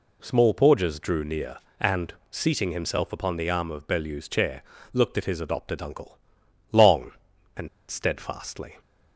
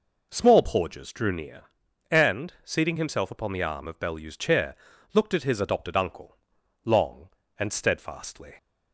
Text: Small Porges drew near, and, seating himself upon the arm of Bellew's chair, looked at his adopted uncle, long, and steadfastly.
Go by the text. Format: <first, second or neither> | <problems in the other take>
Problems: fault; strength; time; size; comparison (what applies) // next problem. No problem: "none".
second | pauses between "and" and "steadfastly"; slight; at 7.6 s; 0.22 s long